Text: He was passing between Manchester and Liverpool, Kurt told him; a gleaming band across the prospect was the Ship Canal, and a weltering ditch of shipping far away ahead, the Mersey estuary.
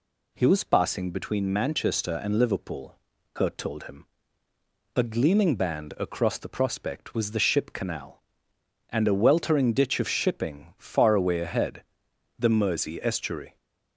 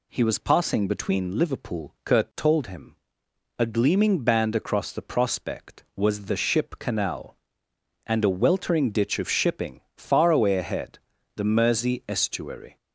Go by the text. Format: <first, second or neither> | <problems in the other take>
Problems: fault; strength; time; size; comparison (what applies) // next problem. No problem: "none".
first | skips "Manchester and"; at 1.3 s